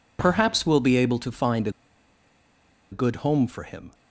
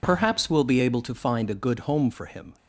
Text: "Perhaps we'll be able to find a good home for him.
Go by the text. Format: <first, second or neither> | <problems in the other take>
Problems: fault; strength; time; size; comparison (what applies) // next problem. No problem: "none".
second | pauses between "a" and "good"; at 1.7 s; 1.2 s long